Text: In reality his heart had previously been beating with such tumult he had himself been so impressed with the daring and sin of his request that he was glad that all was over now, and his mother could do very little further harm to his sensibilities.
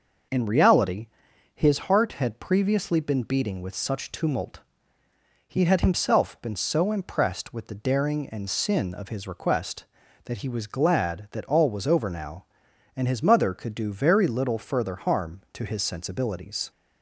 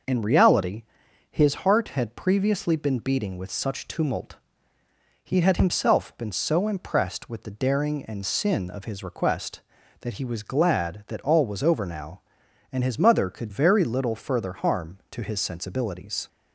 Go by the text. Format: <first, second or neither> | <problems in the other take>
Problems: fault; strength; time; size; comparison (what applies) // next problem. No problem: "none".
first | starts louder than the rest; noticeable; until 1.5 s; 6 dB; noticeable in the first // pauses between "reality" and "his"; noticeable; at 0.8 s; 0.48 s long; noticeable in the first // pauses between "tumult" and "he"; noticeable; at 4.3 s; 0.86 s long; noticeable in the first // skips "do"; at 13.4 s